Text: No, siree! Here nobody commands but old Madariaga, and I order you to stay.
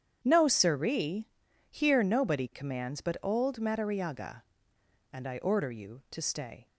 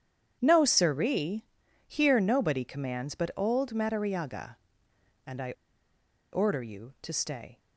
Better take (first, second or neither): first